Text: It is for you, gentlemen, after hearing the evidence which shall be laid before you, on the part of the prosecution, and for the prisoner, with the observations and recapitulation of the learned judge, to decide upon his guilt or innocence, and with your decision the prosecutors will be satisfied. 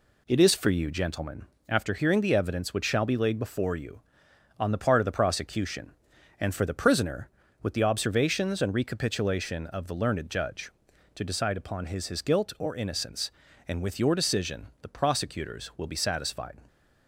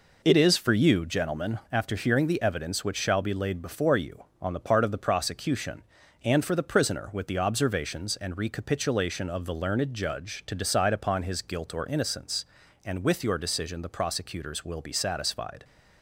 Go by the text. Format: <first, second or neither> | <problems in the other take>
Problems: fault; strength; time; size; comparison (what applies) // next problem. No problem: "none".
second | says "his" twice; at 12.0 s